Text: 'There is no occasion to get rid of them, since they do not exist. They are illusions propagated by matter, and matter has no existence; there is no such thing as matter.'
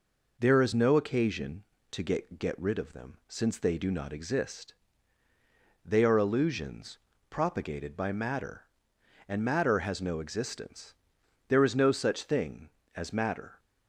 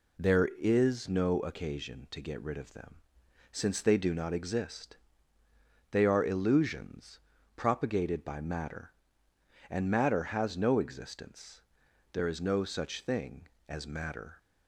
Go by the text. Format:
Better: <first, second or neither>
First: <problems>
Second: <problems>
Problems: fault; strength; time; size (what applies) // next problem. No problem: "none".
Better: second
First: says "get" twice; at 2.3 s // pauses between "illusions" and "propagated"; slight; at 6.9 s; 0.32 s long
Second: pauses between "illusions" and "propagated"; slight; at 7.1 s; 0.36 s long